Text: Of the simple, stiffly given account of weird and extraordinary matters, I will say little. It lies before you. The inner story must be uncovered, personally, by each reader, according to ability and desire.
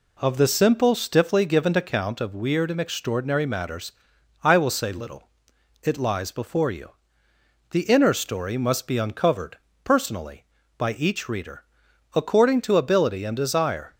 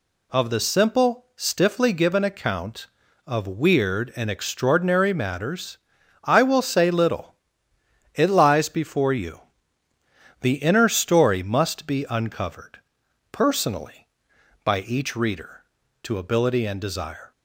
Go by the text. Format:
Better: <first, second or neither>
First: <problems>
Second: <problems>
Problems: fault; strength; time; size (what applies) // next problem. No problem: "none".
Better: first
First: none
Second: skips "according"; at 15.8 s